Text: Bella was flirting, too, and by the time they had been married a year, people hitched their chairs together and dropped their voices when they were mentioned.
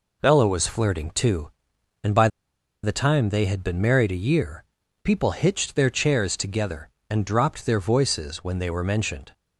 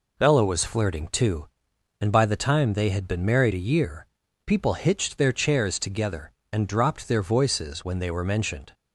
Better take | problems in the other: second | pauses between "by" and "the"; noticeable; at 2.2 s; 0.55 s long

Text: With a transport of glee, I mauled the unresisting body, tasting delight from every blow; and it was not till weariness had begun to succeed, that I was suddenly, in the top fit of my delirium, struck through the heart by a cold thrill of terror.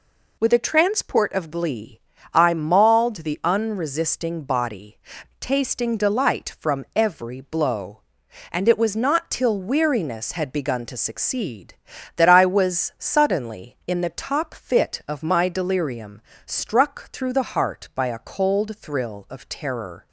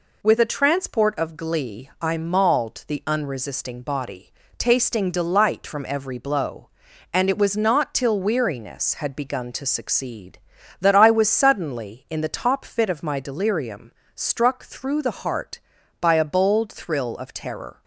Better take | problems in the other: first | says "bold" for "cold"; at 16.2 s

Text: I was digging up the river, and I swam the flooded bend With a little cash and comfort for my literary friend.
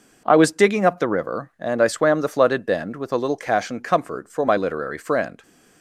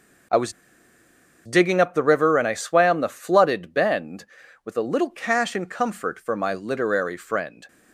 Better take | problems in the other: first | pauses between "was" and "digging"; noticeable; at 0.5 s; 0.92 s long

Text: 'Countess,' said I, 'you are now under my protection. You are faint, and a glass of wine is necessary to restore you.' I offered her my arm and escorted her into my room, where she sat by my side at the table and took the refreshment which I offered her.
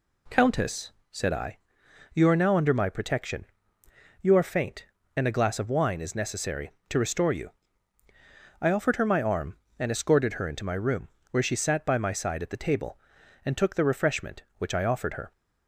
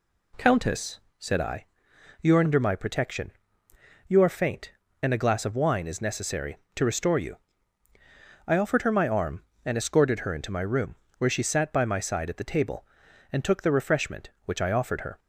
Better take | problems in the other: first | skips "now"; at 2.4 s

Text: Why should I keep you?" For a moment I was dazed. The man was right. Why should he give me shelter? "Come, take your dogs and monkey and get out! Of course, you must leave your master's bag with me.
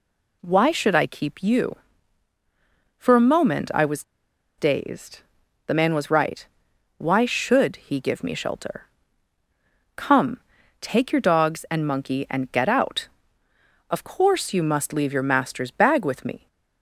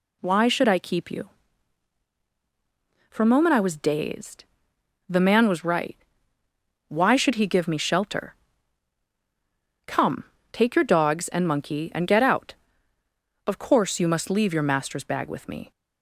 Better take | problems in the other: second | pauses between "was" and "dazed"; noticeable; at 4.0 s; 0.54 s long

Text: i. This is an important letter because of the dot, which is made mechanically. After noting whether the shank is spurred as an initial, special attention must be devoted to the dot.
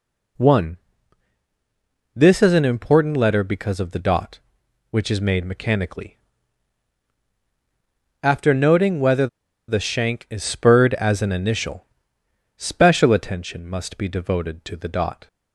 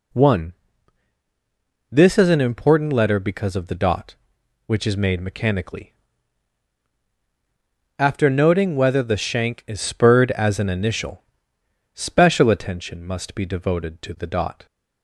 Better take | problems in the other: second | pauses between "whether" and "the"; at 9.2 s; 0.41 s long

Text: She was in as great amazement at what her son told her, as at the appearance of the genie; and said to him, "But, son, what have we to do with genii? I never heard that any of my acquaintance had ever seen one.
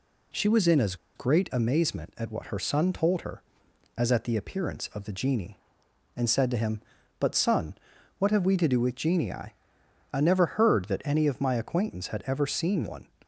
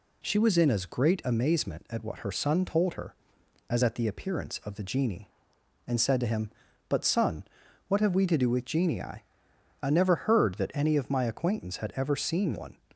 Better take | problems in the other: second | pauses between "as" and "great"; slight; at 0.9 s; 0.20 s long

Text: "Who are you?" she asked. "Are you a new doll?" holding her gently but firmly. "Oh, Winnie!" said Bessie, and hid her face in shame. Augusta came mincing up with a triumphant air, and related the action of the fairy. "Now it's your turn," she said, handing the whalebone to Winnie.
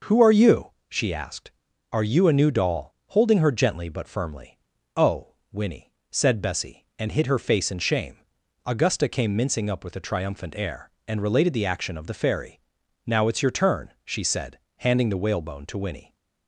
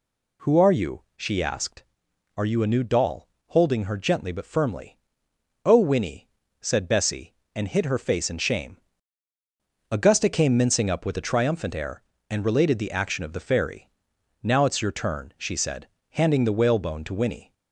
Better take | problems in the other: neither | none

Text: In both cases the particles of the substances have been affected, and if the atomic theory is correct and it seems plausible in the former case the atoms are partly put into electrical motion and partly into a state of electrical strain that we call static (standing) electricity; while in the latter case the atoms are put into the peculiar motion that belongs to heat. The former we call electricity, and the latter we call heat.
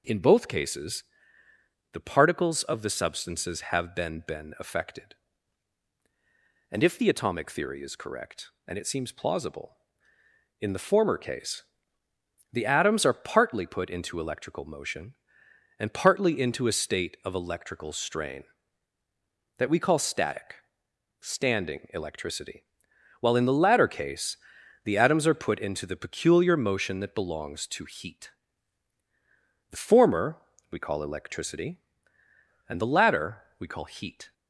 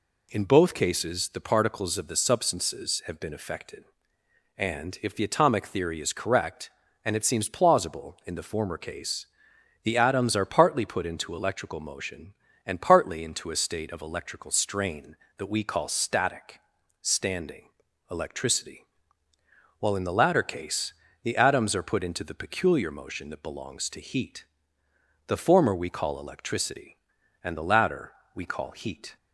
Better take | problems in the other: second | pauses between "cases" and "the"; noticeable; at 1.0 s; 0.88 s long // says "been" twice; at 4.2 s // pauses between "case" and "the"; noticeable; at 11.6 s; 0.90 s long; noticeable in the second // pauses between "case" and "the"; noticeable; at 24.3 s; 0.48 s long; slight in the second // pauses between "former" and "we"; slight; at 30.3 s; 0.34 s long // pauses between "latter" and "we"; slight; at 33.4 s; 0.18 s long; slight in the second

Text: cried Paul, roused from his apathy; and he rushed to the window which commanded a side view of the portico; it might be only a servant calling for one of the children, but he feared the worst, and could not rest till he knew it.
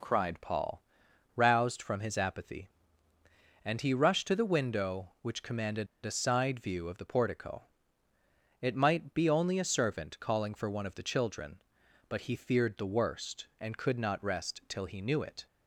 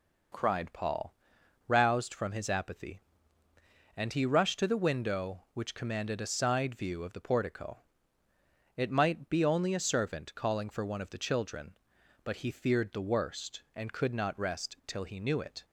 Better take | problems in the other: second | pauses between "commanded" and "a"; slight; at 5.8 s; 0.17 s long

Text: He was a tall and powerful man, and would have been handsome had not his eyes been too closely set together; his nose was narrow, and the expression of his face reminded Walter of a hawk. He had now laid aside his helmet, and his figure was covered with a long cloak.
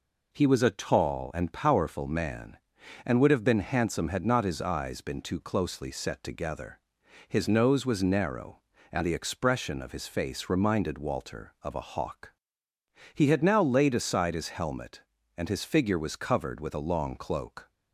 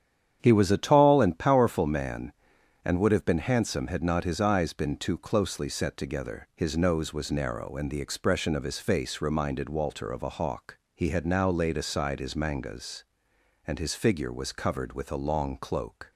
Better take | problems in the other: first | starts louder than the rest; strong; until 1.4 s; 9 dB // says "mangas" for "helmet"; at 12.3 s

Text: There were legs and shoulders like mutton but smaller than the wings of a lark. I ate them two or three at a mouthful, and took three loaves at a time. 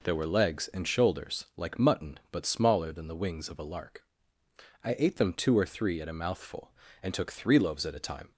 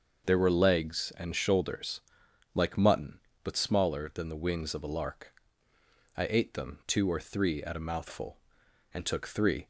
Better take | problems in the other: first | starts louder than the rest; until 1.3 s; 6 dB // pauses between "shoulders" and "like"; noticeable; at 2.0 s; 0.54 s long // stops before "loaves at a time"; at 9.6 s

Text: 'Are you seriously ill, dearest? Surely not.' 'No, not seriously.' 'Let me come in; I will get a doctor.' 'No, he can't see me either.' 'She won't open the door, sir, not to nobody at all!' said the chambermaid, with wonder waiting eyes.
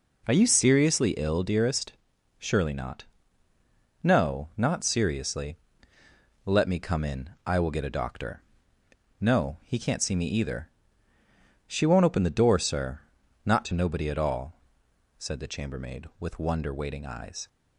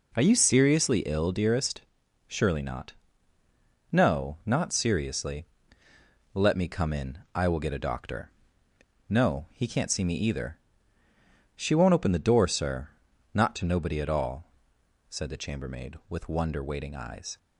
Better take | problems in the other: neither | none

